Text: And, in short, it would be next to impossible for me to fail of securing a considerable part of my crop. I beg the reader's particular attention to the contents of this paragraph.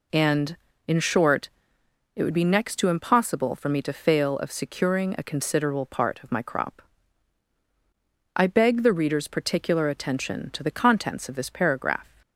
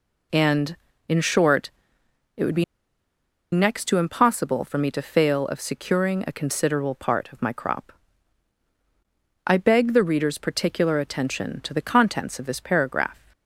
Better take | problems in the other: first | pauses between "be" and "next"; noticeable; at 2.6 s; 0.89 s long

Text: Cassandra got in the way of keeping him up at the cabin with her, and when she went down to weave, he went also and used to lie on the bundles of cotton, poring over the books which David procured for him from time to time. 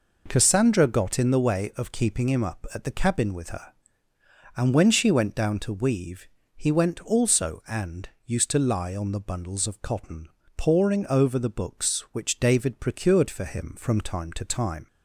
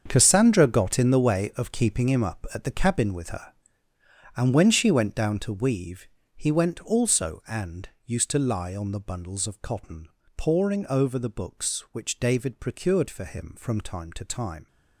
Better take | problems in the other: first | gets quieter; strong; throughout; 12.5 dB // pauses between "and" and "used"; slight; at 7.8 s; 0.16 s long; slight in the first

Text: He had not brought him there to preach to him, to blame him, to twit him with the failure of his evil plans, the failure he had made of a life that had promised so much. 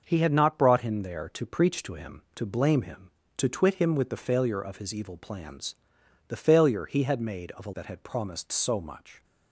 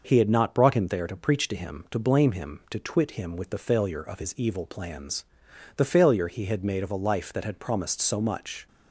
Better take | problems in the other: second | starts louder than the rest; until 1.0 s; 6.5 dB // skips "life"; at 7.7 s

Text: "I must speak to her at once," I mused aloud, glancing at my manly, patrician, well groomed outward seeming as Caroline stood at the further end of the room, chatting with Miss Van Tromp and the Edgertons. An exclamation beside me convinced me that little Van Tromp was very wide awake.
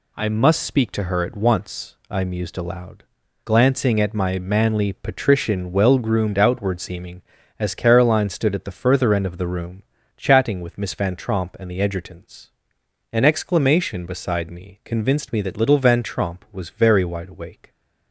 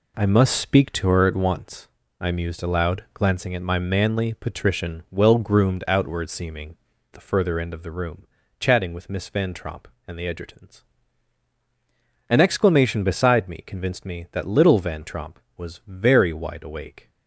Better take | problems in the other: first | skips "as Caroline stood at"; at 6.9 s

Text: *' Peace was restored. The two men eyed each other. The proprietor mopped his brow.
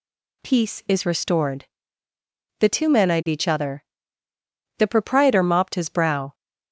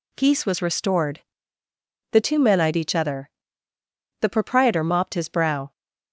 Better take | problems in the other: second | says "is" for "was"; at 0.8 s

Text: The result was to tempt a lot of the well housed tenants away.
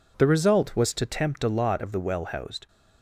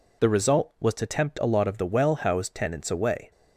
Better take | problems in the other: second | stops before "tenants away"; at 2.6 s

